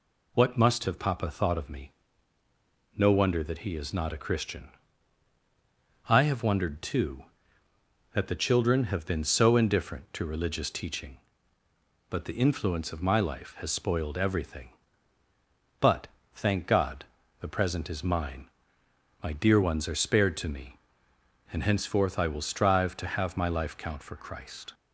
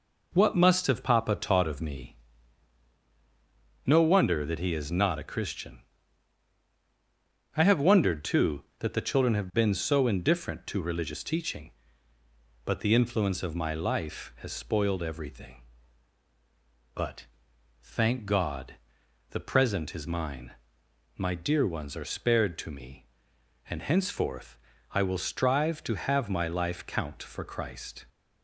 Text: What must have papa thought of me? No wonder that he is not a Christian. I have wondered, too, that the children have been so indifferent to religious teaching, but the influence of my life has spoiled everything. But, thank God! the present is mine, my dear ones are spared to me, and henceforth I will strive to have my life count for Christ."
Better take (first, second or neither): first